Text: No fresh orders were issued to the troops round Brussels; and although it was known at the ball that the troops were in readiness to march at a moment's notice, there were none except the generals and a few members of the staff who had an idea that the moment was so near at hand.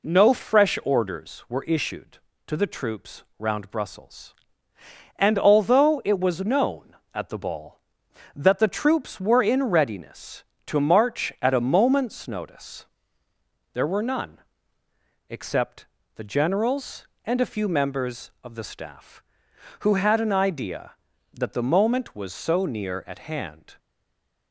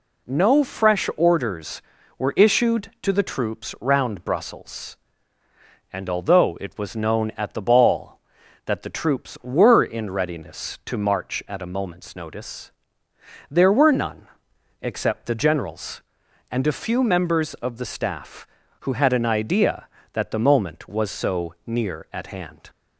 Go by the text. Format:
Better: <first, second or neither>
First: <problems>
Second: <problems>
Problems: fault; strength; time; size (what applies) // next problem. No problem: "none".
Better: second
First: pauses between "troops" and "round"; slight; at 3.2 s; 0.16 s long // pauses between "none" and "except"; noticeable; at 14.3 s; 0.90 s long // pauses between "except" and "the"; slight; at 15.8 s; 0.28 s long // stays silent after the last word; slight; from 23.7 s on; 0.8 s long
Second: pauses between "none" and "except"; noticeable; at 14.2 s; 0.52 s long